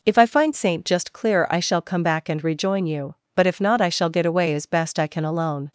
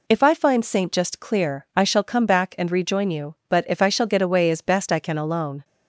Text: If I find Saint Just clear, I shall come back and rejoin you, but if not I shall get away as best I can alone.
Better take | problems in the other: first | skips "not"; at 3.8 s

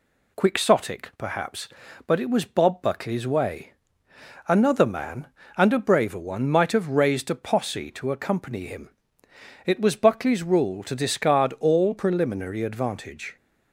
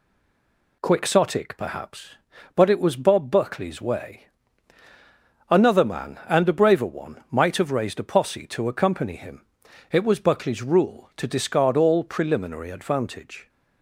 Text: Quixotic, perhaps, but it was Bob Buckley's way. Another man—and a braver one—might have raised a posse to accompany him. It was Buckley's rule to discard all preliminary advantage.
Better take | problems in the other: first | stays silent before the first word; slight; until 0.8 s; 0.8 s long

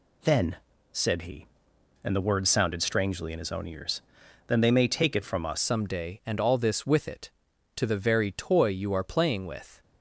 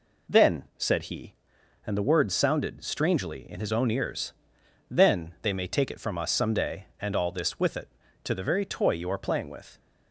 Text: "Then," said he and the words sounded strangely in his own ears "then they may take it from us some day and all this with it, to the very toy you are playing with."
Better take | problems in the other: second | pauses between "ears" and "then"; noticeable; at 4.0 s; 0.46 s long; noticeable in the second // changes voice at "some"; from 5.6 s on; 4.2 s long

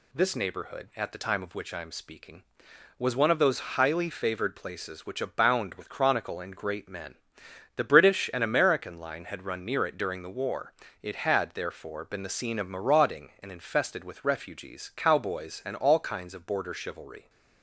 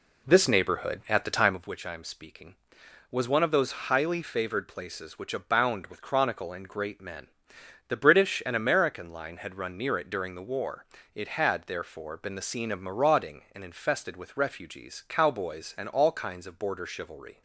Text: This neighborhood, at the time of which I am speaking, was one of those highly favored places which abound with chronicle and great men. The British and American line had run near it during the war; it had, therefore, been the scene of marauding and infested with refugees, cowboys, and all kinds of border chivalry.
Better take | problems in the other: first | starts louder than the rest; slight; until 1.6 s; 2.5 dB

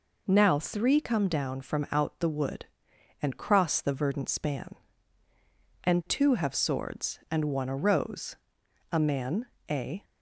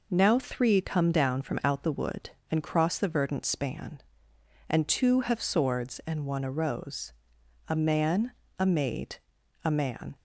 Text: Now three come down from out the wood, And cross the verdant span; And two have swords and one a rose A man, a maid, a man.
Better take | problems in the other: second | pauses between "rose" and "A"; noticeable; at 8.3 s; 0.56 s long; noticeable in the second // stops before "maid a man"; at 10.0 s

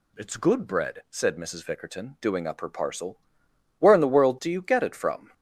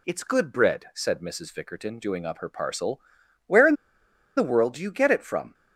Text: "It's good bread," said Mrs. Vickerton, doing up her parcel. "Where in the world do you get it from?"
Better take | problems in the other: first | pauses between "in" and "the"; noticeable; at 3.7 s; 0.64 s long

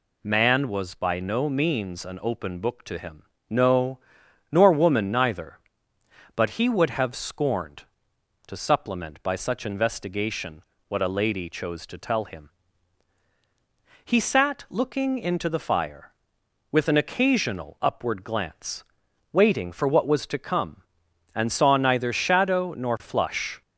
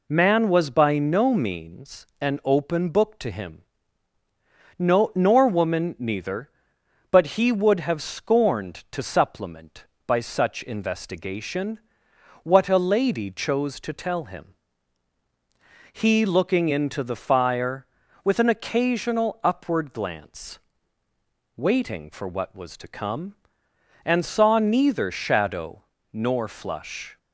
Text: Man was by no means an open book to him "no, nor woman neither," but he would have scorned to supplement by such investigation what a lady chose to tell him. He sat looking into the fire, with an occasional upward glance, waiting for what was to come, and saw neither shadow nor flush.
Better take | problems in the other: first | pauses between "means" and "an"; slight; at 2.0 s; 0.16 s long // pauses between "him" and "no"; at 3.6 s; 1.1 s long; slight in the first // pauses between "investigation" and "what"; noticeable; at 11.7 s; 0.66 s long; slight in the first // skips "sat"; at 16.2 s // pauses between "shadow" and "nor"; slight; at 25.8 s; 0.32 s long

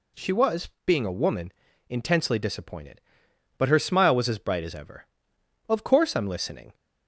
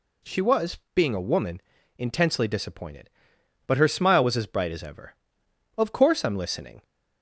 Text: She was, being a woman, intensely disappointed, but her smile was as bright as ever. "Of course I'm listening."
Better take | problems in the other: neither | none

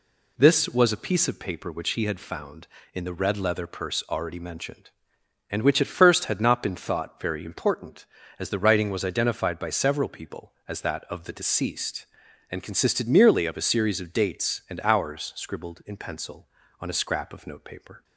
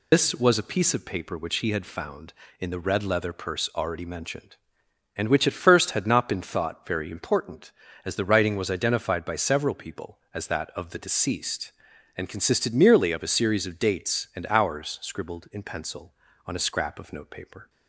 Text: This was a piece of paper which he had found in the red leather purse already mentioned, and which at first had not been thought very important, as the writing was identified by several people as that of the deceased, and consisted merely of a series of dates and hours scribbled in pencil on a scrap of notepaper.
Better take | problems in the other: first | loses the start of "This"; at 0.1 s; 85 ms

